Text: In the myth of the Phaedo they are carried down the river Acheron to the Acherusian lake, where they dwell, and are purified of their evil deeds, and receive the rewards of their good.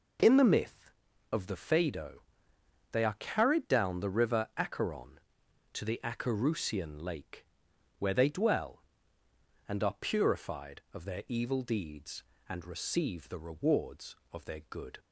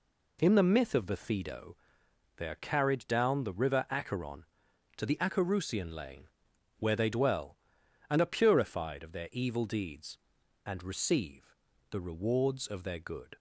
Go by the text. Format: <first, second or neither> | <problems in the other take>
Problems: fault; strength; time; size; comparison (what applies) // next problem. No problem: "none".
first | pauses between "Phaedo" and "they"; noticeable; at 1.7 s; 0.62 s long; noticeable in the first // says "lane" for "lake"; at 5.9 s // pauses between "receive" and "the"; slight; at 11.5 s; 0.36 s long